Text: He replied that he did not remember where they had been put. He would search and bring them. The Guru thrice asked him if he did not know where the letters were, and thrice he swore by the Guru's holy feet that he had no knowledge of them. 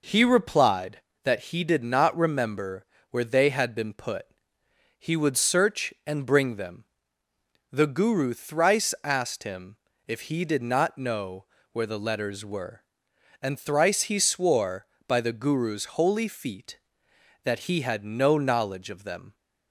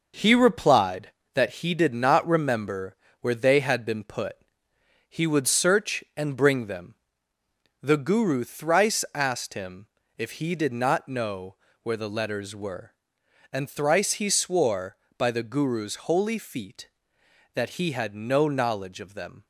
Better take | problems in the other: first | gets quieter; noticeable; throughout; 5.5 dB // pauses between "remember" and "where"; slight; at 2.9 s; 0.24 s long; slight in the first // pauses between "him" and "if"; slight; at 9.8 s; 0.30 s long; slight in the first // pauses between "know" and "where"; slight; at 11.5 s; 0.26 s long; slight in the first

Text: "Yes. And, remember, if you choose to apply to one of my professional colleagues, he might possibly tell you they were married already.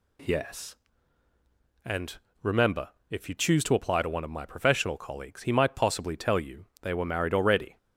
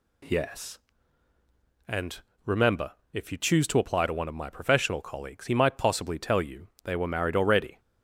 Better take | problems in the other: neither | pauses between "you" and "they"; slight; the same in both

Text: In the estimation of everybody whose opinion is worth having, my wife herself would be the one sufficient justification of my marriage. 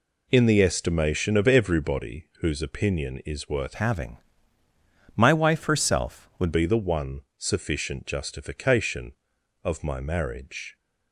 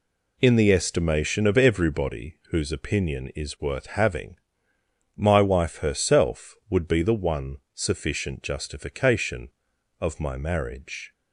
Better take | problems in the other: second | changes voice from "having" to "would"; from 3.7 to 6.5 s; 2.8 s long // pauses between "one" and "sufficient"; slight; at 7.2 s; 0.16 s long; slight in the second

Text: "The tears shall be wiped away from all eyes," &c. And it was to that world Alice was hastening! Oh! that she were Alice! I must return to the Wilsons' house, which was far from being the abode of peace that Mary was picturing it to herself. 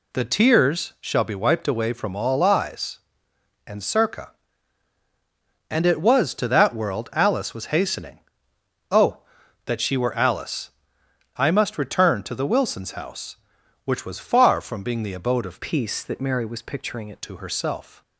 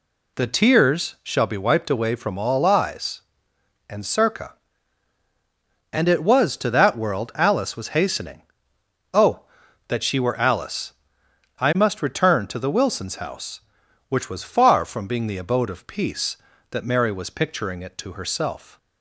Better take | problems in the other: second | changes voice from "peace" to "it"; from 15.6 to 17.1 s; 1.5 s long

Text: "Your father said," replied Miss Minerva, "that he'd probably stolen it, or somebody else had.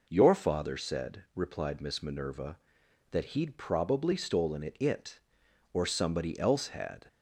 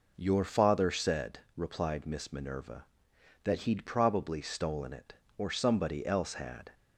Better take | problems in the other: second | says "it" twice; at 4.7 s

